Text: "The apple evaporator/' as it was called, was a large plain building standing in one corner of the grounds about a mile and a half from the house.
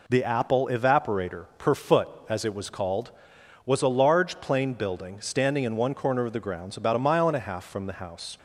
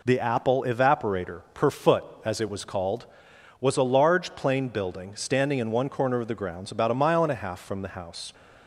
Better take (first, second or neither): neither